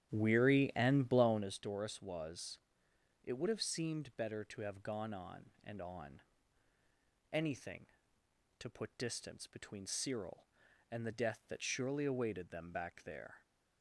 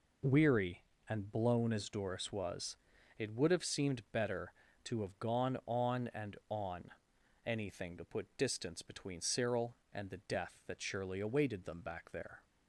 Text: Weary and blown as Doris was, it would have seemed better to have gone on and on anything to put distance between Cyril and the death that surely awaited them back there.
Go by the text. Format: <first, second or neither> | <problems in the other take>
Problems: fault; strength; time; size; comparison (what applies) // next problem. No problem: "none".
second | starts louder than the rest; strong; until 1.5 s; 10 dB // pauses between "on" and "anything"; at 6.1 s; 1.1 s long; noticeable in the second